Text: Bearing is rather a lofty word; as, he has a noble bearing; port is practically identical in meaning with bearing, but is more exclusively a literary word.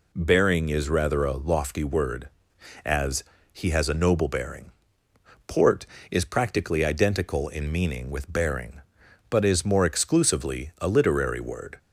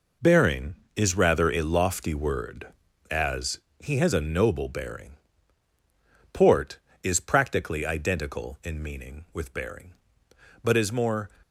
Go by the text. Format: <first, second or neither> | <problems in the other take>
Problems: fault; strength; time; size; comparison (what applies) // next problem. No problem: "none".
first | stops before "exclusively a literary word"; at 11.4 s